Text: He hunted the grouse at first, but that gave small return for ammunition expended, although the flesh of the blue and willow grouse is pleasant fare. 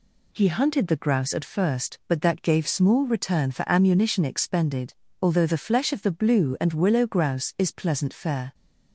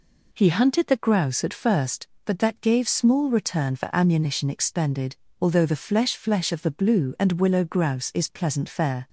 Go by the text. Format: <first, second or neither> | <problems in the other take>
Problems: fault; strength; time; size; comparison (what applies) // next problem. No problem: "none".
first | says "flesh" twice; at 6.1 s